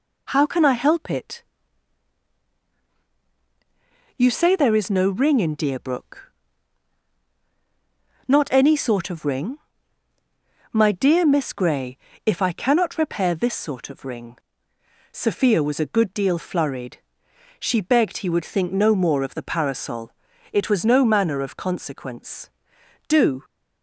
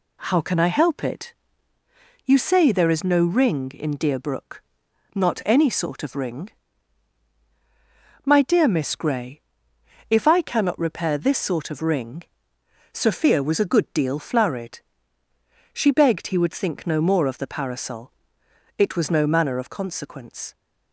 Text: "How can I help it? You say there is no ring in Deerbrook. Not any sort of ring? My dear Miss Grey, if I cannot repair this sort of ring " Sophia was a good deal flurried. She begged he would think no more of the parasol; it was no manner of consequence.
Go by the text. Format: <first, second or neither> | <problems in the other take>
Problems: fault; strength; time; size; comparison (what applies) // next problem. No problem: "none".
second | goes on to say "Do"; slight; from 23.0 s on; 0.36 s long